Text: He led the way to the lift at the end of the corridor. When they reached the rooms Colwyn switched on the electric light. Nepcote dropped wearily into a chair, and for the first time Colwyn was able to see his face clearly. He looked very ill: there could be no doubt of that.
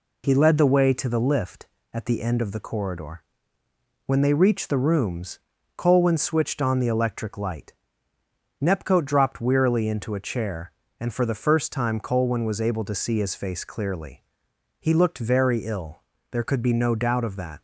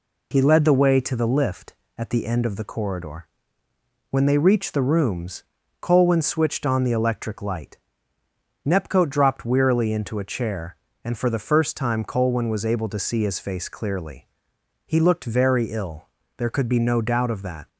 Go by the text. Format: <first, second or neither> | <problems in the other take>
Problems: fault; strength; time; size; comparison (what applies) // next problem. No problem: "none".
neither | pauses between "rooms" and "Colwyn"; the same in both